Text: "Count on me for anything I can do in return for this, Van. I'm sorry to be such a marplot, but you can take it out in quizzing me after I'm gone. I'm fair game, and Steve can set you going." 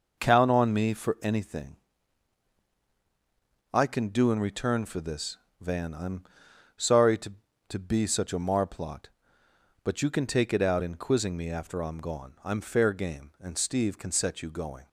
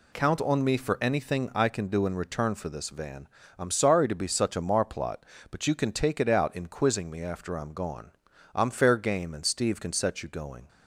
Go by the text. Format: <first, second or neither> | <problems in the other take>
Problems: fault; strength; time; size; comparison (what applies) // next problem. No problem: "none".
second | pauses between "anything" and "I"; strong; at 1.7 s; 1.9 s long // pauses between "I'm" and "sorry"; noticeable; at 6.2 s; 0.52 s long // says "to" twice; at 7.6 s